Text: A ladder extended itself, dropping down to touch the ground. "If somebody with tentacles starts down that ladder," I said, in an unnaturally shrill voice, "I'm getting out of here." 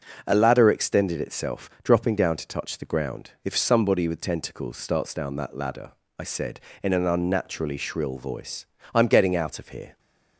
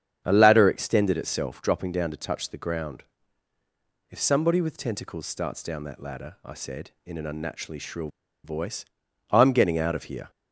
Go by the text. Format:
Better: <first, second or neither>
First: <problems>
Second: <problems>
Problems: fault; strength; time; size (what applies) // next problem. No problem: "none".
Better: first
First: none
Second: starts louder than the rest; strong; until 1.2 s; 8 dB // pauses between "shrill" and "voice"; slight; at 8.0 s; 0.35 s long